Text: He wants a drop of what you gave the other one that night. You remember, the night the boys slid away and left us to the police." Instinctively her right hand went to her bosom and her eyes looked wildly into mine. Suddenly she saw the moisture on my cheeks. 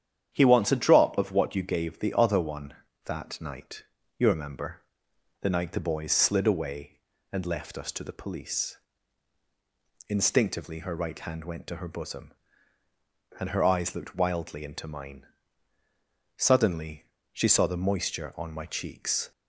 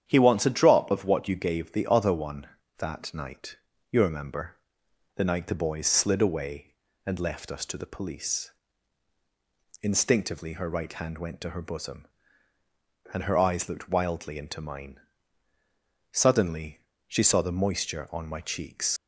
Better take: first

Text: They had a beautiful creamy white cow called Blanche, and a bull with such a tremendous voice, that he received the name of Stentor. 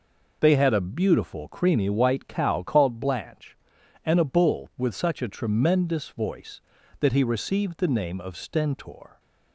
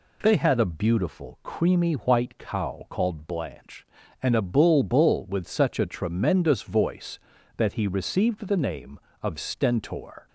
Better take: first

